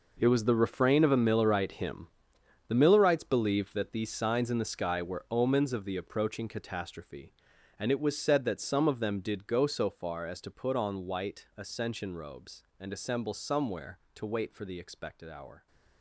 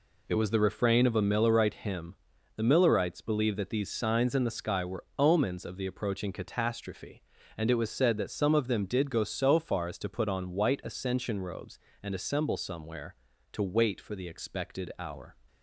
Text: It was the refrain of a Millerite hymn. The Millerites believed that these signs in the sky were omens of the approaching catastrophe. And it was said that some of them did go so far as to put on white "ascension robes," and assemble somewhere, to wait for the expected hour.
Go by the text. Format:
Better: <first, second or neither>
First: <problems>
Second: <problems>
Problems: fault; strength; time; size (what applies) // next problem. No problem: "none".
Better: second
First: gets quieter; strong; throughout; 13 dB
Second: none